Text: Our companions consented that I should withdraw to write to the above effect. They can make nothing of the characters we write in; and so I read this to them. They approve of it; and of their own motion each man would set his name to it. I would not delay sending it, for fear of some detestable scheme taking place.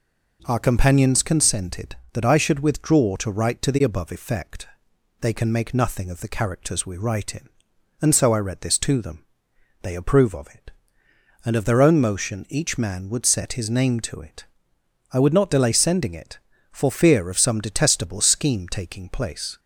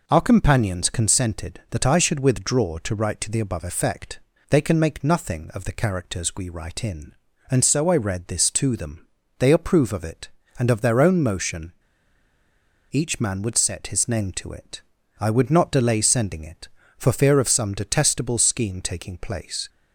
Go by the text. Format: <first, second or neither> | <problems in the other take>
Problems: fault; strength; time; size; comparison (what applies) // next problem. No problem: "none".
first | pauses between "motion" and "each"; at 11.7 s; 1.1 s long